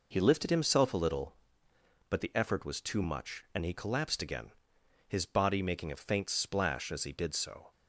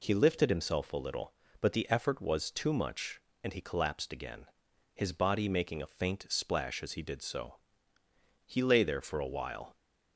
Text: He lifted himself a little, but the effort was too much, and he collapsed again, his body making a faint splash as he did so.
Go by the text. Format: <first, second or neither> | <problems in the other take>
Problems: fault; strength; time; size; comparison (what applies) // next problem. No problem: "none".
first | goes on to say "He lay there for a while"; noticeable; from 8.4 s on; 1.2 s long